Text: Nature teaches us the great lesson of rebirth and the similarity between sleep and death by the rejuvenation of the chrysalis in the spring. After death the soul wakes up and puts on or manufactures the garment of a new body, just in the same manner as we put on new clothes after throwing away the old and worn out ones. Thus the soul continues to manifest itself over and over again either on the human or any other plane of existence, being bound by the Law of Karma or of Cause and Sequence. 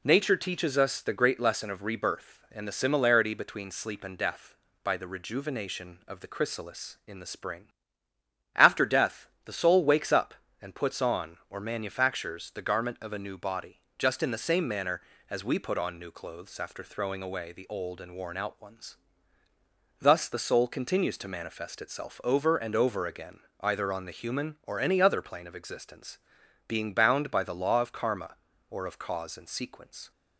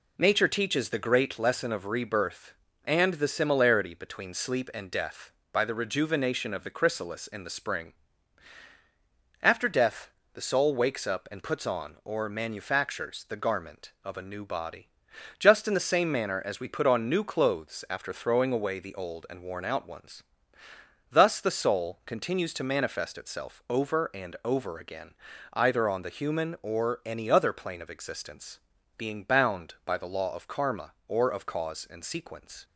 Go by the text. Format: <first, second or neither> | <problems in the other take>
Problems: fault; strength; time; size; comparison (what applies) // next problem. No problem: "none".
first | skips "us"; at 0.8 s // pauses between "death" and "the"; slight; at 10.1 s; 0.22 s long; slight in the first // pauses between "again" and "either"; at 25.1 s; 0.40 s long; slight in the first